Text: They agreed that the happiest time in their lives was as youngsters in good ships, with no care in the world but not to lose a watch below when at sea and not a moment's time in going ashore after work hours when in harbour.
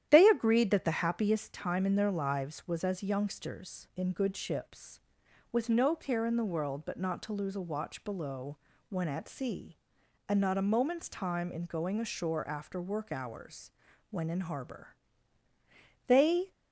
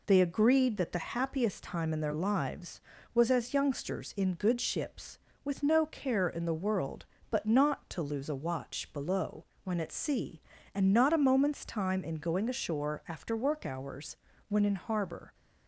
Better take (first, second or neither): second